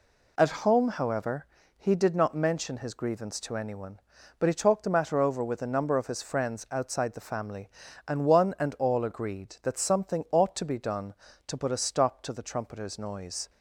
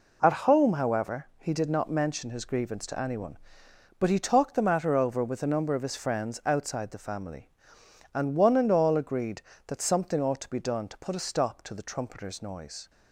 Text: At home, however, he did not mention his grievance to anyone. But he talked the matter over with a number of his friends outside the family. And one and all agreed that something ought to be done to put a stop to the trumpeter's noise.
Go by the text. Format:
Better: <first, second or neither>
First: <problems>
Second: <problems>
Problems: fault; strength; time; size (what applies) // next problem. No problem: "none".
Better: neither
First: none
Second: none